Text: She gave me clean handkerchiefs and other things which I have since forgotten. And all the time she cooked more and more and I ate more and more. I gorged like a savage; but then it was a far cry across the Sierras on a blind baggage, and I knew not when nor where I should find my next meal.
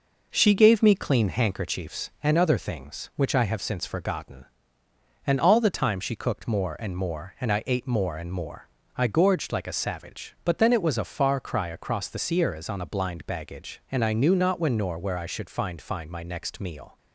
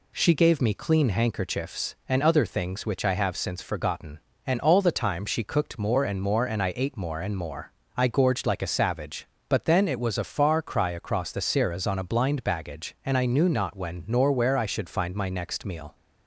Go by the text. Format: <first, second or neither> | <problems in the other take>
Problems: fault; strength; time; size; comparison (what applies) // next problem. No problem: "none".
second | says "find" twice; at 15.7 s